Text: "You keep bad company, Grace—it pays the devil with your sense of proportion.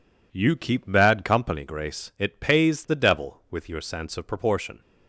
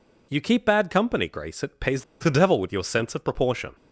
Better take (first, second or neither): first